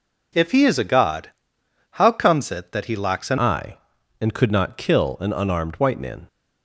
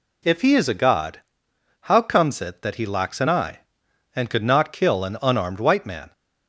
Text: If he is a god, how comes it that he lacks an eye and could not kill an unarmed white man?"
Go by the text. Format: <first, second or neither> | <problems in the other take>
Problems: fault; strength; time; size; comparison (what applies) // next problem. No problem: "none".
second | changes voice at "eye"; from 3.3 s on; 2.9 s long